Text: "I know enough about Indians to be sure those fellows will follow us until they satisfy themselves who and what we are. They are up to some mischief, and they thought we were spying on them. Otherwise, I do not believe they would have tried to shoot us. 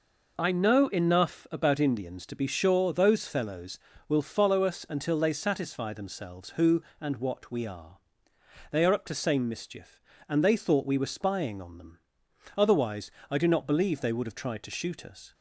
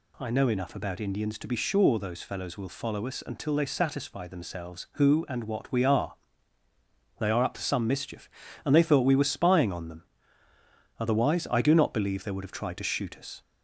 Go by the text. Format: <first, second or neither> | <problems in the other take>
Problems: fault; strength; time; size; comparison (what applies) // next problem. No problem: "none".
second | says "same" for "some"; at 9.1 s